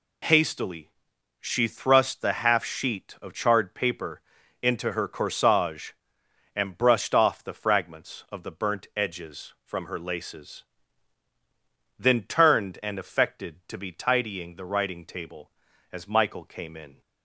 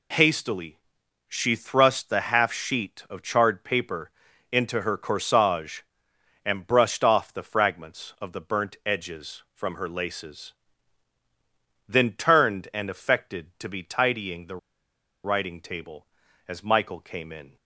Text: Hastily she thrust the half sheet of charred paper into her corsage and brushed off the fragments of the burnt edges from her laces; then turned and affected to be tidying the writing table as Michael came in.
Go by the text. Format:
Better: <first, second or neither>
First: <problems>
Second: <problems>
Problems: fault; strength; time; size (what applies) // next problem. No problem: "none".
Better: first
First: pauses between "Hastily" and "she"; noticeable; at 0.8 s; 0.52 s long // pauses between "paper" and "into"; at 4.2 s; 0.40 s long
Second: pauses between "Hastily" and "she"; noticeable; at 0.7 s; 0.52 s long // pauses between "paper" and "into"; at 4.1 s; 0.40 s long // pauses between "the" and "writing"; noticeable; at 14.5 s; 0.67 s long